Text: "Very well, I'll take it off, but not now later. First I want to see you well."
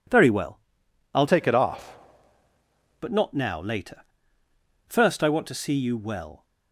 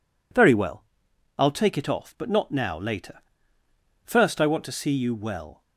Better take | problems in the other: second | changes voice from "take" to "off"; from 1.2 to 1.9 s; 0.7 s long

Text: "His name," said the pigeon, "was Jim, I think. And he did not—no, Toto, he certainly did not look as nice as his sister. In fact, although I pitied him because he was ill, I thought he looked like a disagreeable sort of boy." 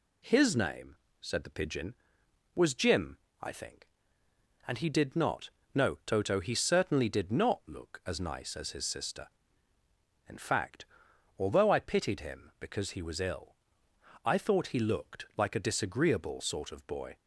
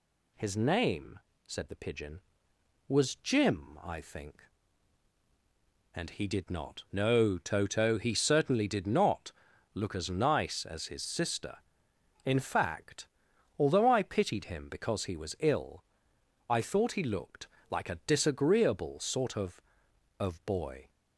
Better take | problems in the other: first | pauses between "not" and "look"; at 9.3 s; 0.42 s long // pauses between "looked" and "like"; slight; at 17.4 s; 0.22 s long // says "of" twice; at 20.1 s

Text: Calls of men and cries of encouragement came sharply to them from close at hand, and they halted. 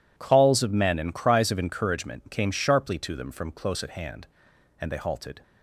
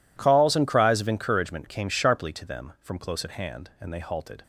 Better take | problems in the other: first | skips "of men"; at 0.5 s

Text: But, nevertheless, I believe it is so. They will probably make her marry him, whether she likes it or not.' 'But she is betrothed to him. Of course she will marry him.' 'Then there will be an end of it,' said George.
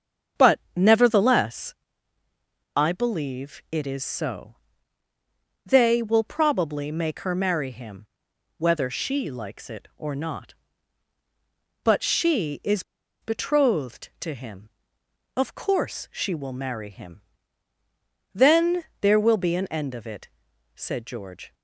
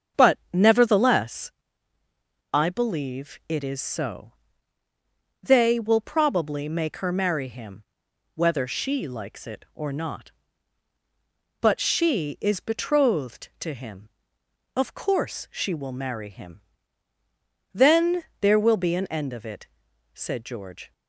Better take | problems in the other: second | starts louder than the rest; until 1.5 s; 7 dB; also in the second // pauses between "is" and "betrothed"; at 12.8 s; 0.39 s long // pauses between "Then" and "there"; slight; at 18.8 s; 0.16 s long; slight in the second

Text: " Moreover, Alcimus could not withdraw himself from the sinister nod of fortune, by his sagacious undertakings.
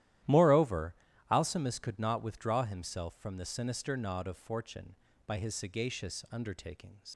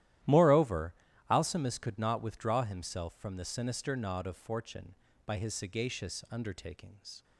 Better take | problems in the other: second | starts louder than the rest; strong; until 1.5 s; 13 dB; strong in the second // leaves "undertakings" unfinished; at 7.1 s; 95 ms

